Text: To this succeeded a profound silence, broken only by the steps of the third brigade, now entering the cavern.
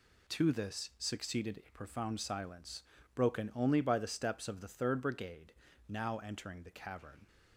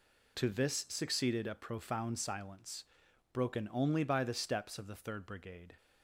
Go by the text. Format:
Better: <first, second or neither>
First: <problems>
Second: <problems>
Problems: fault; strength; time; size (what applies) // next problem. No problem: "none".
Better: first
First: none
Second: stops before "now entering the cavern"; at 5.7 s